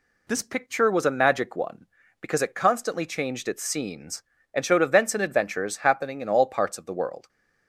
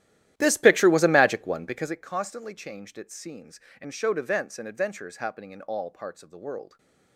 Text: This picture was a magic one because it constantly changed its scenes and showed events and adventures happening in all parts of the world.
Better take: first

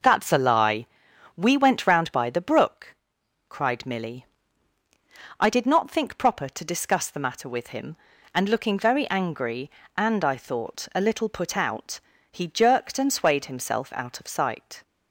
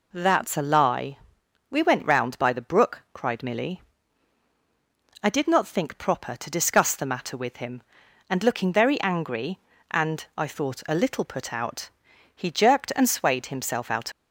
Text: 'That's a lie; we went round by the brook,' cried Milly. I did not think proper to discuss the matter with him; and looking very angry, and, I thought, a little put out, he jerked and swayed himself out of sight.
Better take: first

